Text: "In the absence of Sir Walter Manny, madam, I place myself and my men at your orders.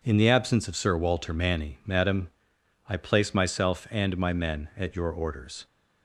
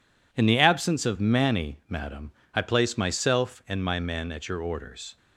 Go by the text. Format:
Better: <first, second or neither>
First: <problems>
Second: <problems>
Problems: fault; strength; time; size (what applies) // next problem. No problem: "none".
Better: first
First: none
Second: skips "Sir Walter"; at 1.1 s